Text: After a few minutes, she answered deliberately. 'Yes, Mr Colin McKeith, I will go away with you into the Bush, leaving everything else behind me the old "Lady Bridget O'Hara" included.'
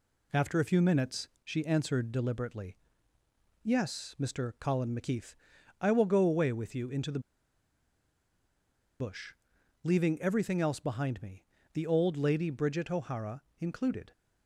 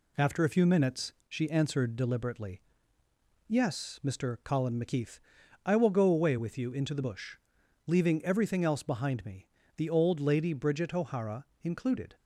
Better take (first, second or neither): second